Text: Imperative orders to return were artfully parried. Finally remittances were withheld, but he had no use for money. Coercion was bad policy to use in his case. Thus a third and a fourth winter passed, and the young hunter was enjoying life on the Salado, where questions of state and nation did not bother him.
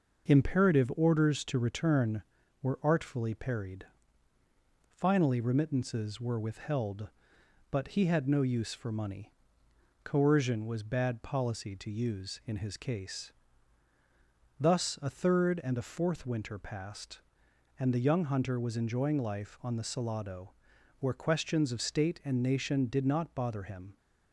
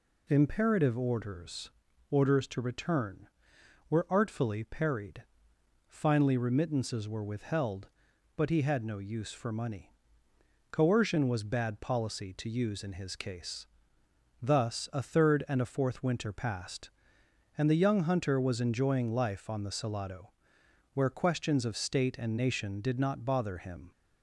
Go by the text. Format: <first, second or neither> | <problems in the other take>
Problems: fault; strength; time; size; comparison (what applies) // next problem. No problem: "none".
first | says "orders" twice; at 2.1 s